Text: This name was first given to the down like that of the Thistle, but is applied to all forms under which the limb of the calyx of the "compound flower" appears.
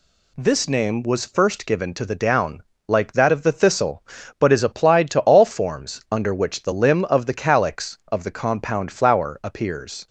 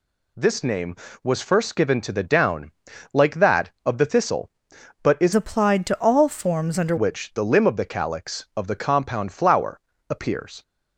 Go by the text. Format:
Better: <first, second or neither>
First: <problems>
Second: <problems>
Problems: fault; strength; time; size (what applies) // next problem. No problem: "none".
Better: first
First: pauses between "down" and "like"; slight; at 2.6 s; 0.24 s long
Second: pauses between "down" and "like"; at 2.7 s; 0.42 s long // changes voice from "applied" to "under"; from 5.3 to 6.9 s; 1.6 s long // pauses between "flower" and "appears"; slight; at 9.8 s; 0.28 s long